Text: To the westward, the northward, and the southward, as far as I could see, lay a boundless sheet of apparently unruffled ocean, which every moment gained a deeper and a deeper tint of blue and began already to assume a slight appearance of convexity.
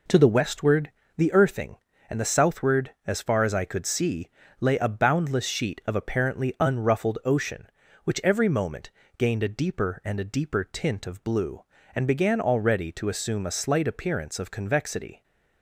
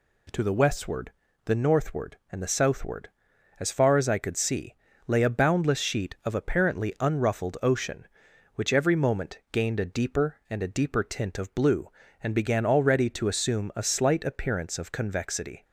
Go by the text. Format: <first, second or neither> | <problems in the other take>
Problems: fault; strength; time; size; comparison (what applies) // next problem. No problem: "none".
second | says "earthing" for "northward"; at 1.3 s // pauses between "moment" and "gained"; slight; at 8.8 s; 0.28 s long